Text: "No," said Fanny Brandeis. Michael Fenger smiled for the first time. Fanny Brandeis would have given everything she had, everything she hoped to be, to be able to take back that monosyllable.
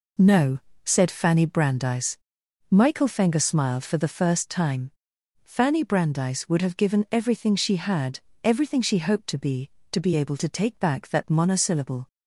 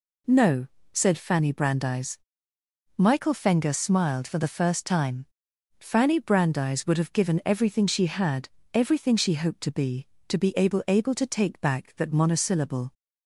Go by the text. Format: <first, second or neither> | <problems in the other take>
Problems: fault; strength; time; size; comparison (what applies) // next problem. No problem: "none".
first | says "able" twice; at 10.8 s